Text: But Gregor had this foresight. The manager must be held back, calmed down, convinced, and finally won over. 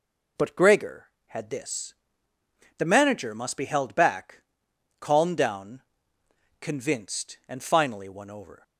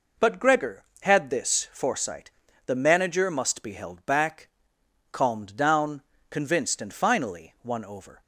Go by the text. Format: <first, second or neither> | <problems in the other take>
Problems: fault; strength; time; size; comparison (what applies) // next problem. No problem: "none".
second | skips "foresight"; at 2.3 s